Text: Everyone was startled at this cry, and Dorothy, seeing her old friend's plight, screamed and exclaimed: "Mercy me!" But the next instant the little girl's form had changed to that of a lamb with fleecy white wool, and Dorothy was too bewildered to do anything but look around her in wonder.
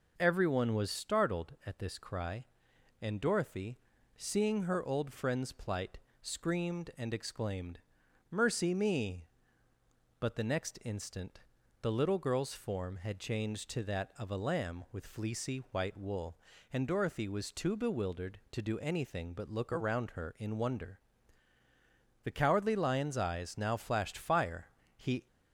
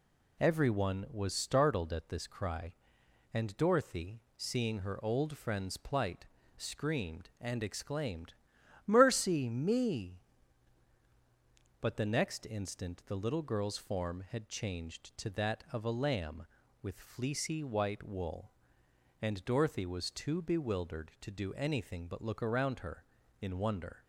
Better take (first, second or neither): second